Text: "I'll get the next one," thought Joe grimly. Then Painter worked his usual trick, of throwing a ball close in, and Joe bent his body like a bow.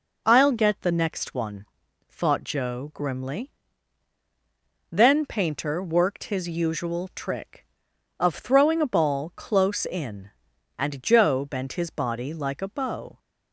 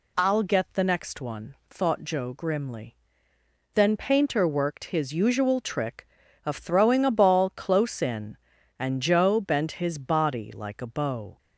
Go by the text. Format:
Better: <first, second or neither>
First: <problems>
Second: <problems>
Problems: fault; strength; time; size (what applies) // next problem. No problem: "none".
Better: neither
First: none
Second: none